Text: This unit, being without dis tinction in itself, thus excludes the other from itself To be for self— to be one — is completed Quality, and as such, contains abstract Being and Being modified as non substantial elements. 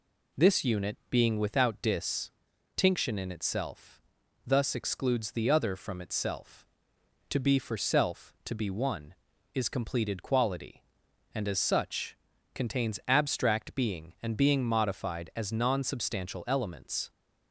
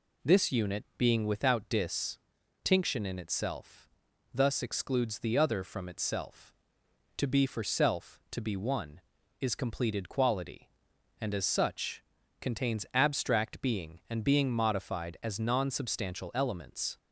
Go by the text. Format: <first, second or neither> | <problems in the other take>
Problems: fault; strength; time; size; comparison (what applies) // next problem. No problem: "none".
neither | pauses between "dis" and "tinction"; the same in both